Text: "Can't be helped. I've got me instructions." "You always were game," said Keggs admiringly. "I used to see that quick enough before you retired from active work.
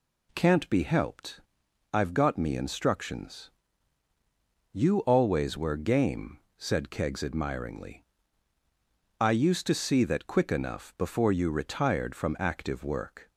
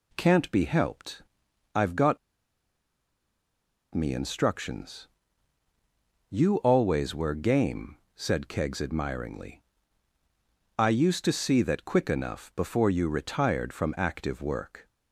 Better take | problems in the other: first | pauses between "got" and "me"; strong; at 2.1 s; 1.7 s long

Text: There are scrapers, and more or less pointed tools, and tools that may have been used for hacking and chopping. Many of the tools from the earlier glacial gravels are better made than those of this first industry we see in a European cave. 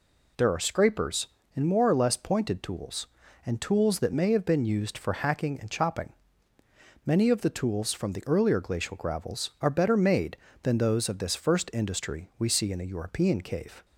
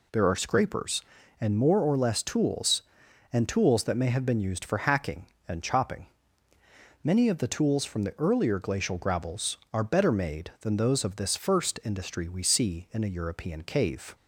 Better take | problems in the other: first | skips "pointed"; at 2.2 s

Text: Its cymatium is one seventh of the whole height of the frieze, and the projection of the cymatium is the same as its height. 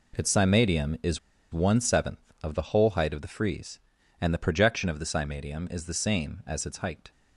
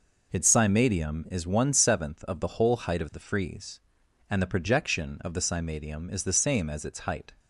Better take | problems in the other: second | pauses between "is" and "one"; slight; at 1.1 s; 0.33 s long

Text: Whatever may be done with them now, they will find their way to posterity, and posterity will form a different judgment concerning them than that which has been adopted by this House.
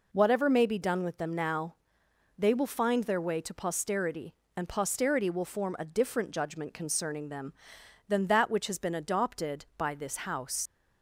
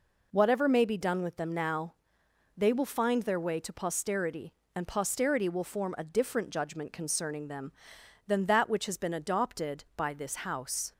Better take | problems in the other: second | leaves "House" unfinished; at 10.6 s; 80 ms

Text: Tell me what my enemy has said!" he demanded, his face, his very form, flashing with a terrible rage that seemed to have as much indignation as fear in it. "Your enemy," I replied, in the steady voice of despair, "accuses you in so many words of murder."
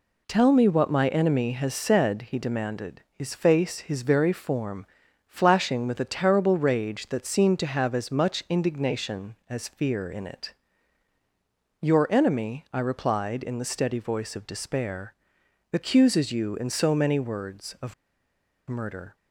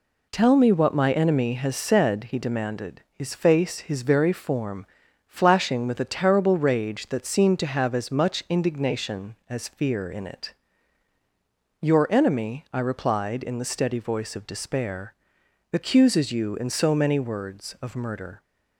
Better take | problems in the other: second | pauses between "of" and "murder"; noticeable; at 17.9 s; 0.74 s long

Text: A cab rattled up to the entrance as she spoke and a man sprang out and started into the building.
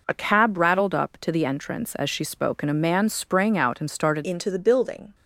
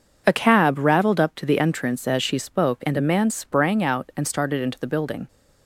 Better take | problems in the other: second | changes voice at "into"; from 4.2 s on; 0.9 s long

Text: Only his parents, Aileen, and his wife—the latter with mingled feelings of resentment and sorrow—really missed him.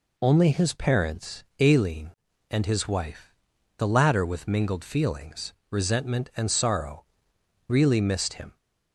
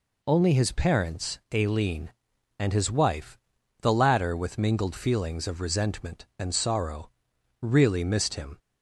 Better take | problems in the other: second | skips "of"; at 5.6 s

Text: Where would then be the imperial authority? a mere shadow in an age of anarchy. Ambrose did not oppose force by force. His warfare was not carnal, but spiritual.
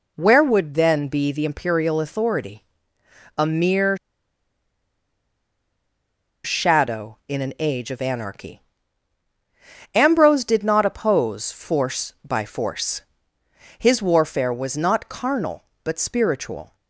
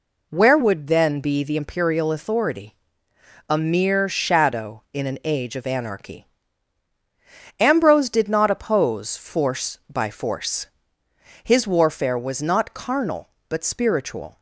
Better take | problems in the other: second | pauses between "mere" and "shadow"; strong; at 3.9 s; 2.4 s long

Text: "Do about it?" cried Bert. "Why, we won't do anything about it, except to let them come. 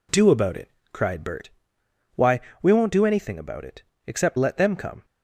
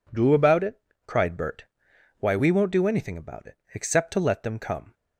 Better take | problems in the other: second | skips "to"; at 4.3 s

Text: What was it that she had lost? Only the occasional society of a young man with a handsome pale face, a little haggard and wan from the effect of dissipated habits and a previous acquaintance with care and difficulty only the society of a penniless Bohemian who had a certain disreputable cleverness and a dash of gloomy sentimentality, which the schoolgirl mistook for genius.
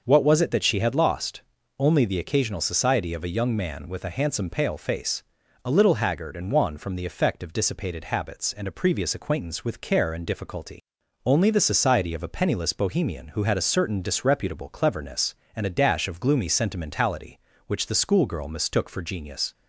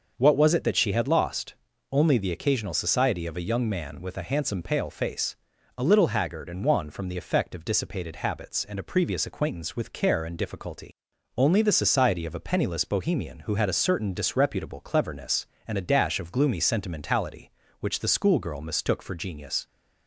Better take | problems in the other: neither | starts louder than the rest; noticeable; the same in both // pauses between "difficulty" and "only"; noticeable; the same in both

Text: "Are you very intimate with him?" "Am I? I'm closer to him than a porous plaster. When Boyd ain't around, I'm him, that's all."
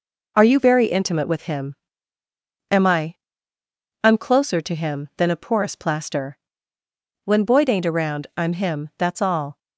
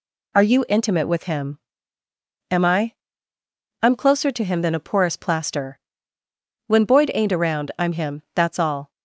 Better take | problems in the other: first | skips "very"; at 0.6 s

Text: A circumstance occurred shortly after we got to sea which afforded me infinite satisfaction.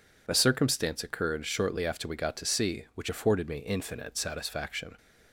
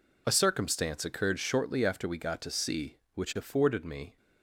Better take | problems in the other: first | stops before "infinite satisfaction"; at 4.1 s

